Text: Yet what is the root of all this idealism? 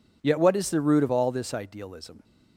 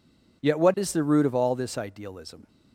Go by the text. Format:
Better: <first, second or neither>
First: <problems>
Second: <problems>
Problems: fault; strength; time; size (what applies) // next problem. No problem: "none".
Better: neither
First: none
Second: none